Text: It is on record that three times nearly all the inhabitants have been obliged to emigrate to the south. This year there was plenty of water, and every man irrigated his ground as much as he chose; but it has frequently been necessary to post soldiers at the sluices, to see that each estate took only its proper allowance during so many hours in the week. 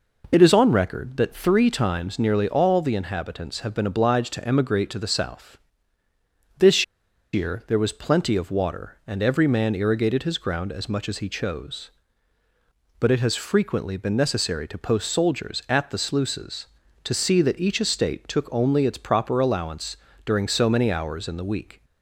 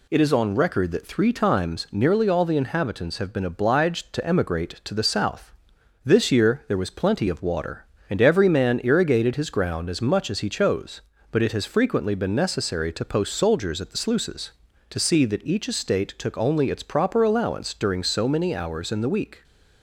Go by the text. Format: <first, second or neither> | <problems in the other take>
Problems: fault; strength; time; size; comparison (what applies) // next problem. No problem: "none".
second | pauses between "This" and "year"; noticeable; at 6.8 s; 0.49 s long // pauses between "allowance" and "during"; slight; at 19.9 s; 0.30 s long